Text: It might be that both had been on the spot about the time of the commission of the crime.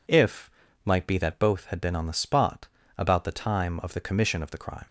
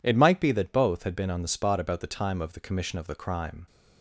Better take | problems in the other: second | says "If" for "It"; at 0.0 s // pauses between "spot" and "about"; slight; at 2.6 s; 0.32 s long

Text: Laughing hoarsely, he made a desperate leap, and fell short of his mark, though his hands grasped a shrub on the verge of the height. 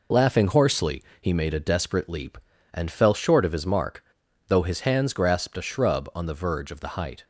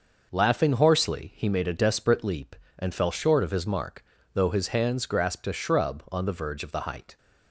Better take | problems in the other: neither | none

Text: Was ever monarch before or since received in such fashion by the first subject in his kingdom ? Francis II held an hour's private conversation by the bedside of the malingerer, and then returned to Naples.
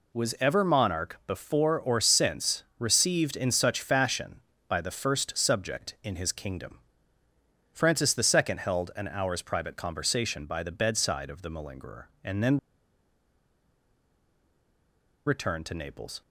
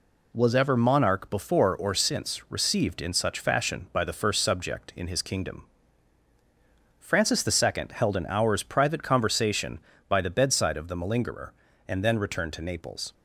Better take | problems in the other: second | pauses between "since" and "received"; slight; at 2.6 s; 0.16 s long // pauses between "then" and "returned"; strong; at 12.5 s; 2.7 s long

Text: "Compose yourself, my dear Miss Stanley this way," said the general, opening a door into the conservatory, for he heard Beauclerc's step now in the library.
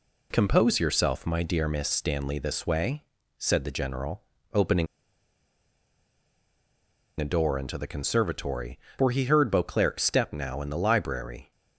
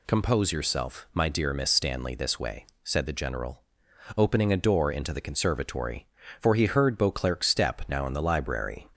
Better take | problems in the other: second | pauses between "opening" and "a"; strong; at 4.8 s; 2.3 s long

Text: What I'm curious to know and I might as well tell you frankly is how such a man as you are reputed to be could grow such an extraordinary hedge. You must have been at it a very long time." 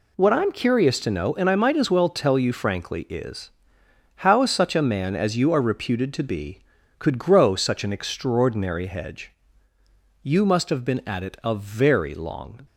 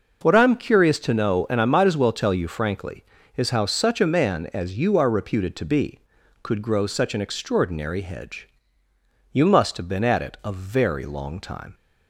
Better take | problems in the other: second | pauses between "is" and "how"; noticeable; at 3.4 s; 0.66 s long // stops before "time"; at 12.6 s

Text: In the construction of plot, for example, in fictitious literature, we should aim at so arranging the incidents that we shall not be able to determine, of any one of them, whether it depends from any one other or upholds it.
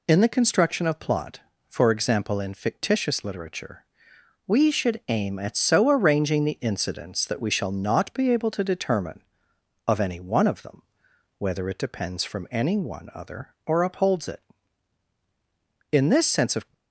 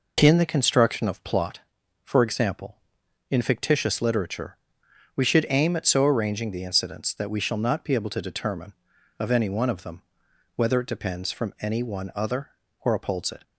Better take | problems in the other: second | goes on to say "In this sense of"; noticeable; from 15.8 s on; 0.84 s long

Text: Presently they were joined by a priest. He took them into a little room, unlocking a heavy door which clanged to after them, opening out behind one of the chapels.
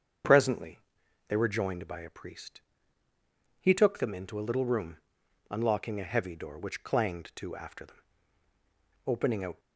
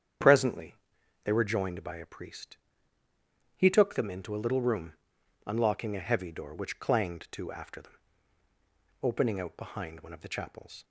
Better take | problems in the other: second | starts louder than the rest; strong; until 1.7 s; 7.5 dB; strong in the second // pauses between "Presently" and "they"; noticeable; at 0.7 s; 0.48 s long; noticeable in the second // stops before "behind one of the chapels"; at 9.5 s

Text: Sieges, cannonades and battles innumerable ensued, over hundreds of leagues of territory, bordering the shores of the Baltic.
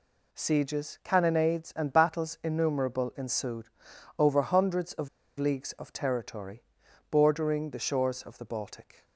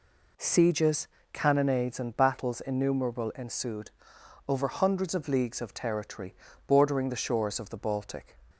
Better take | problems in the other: second | pauses between "of" and "leagues"; slight; at 5.0 s; 0.31 s long

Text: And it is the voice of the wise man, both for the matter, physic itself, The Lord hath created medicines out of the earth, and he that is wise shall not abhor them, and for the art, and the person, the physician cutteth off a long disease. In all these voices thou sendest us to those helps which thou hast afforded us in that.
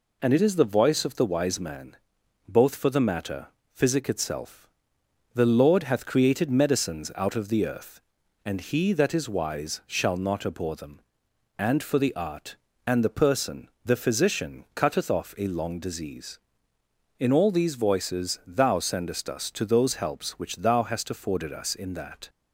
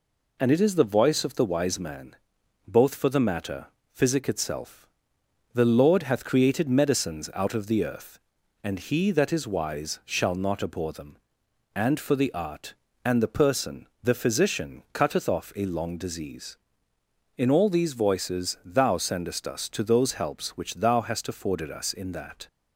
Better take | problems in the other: neither | none

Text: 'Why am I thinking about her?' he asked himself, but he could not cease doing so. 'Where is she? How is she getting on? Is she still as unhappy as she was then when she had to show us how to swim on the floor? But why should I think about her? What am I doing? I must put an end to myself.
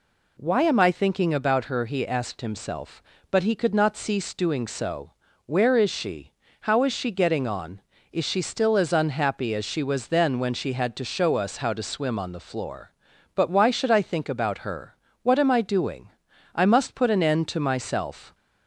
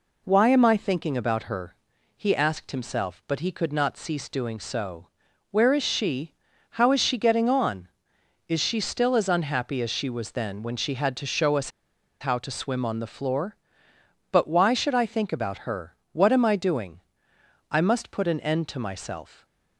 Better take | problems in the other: first | pauses between "us" and "how"; noticeable; at 11.6 s; 0.51 s long

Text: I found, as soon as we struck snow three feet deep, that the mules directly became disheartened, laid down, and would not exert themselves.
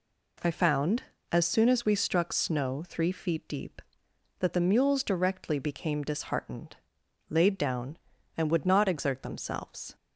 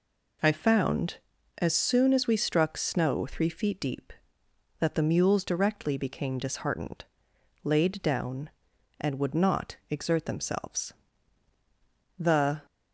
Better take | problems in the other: first | goes on to say "The"; slight; from 12.1 s on; 0.46 s long

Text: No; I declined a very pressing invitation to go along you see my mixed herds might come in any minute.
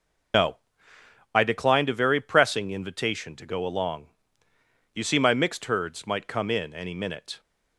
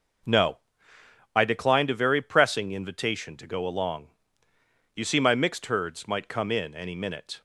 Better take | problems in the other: second | loses the start of "No"; at 0.3 s; 100 ms // pauses between "along" and "you"; noticeable; at 4.0 s; 0.88 s long; noticeable in the second

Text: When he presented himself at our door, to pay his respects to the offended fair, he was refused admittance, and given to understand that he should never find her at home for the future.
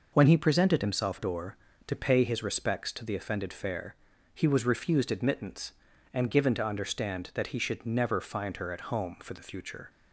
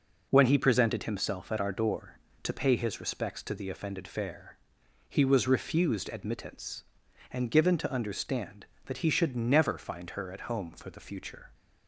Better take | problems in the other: second | skips "at our"; at 1.1 s

